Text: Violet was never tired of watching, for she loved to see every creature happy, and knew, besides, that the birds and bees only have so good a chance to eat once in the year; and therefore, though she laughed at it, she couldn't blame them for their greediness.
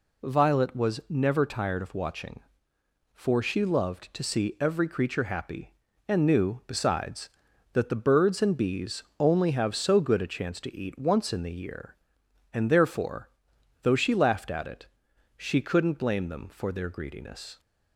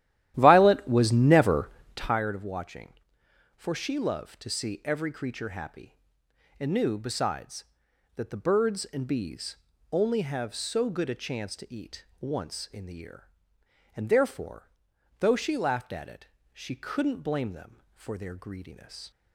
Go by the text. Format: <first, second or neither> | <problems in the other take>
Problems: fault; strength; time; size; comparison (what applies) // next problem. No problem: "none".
first | starts louder than the rest; strong; until 2.2 s; 13 dB // pauses between "never" and "tired"; slight; at 1.6 s; 0.26 s long // pauses between "bees" and "only"; slight; at 9.5 s; 0.34 s long; slight in the first